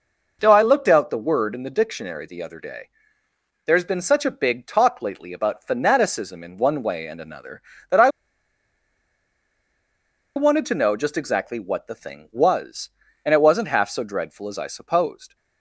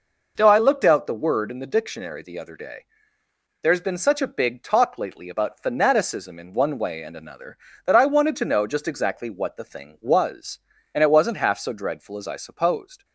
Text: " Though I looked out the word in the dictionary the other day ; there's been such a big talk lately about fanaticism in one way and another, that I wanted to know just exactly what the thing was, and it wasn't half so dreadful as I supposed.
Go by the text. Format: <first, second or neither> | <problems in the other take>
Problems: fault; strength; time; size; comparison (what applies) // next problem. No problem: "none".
second | pauses between "I" and "wanted"; strong; at 8.0 s; 2.2 s long